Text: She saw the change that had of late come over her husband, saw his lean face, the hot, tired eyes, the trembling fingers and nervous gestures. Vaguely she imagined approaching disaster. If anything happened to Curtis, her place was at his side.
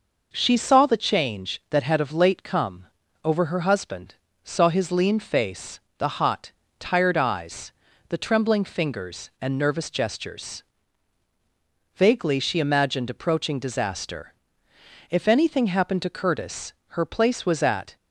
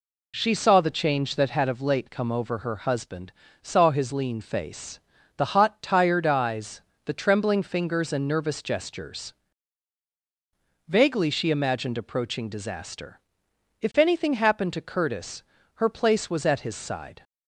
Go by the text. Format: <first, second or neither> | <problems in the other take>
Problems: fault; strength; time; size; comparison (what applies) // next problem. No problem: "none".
second | pauses between "come" and "over"; slight; at 2.8 s; 0.36 s long // stops before "his side"; at 17.9 s